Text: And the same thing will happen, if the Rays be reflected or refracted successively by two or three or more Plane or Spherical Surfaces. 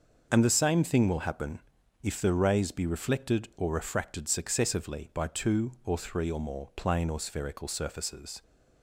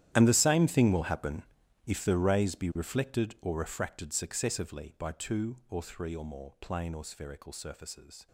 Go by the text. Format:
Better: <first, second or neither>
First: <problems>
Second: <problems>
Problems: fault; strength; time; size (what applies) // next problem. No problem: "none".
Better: first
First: starts louder than the rest; until 1.3 s; 6.5 dB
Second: gets quieter; strong; throughout; 18.5 dB // starts louder than the rest; strong; until 1.1 s; 12 dB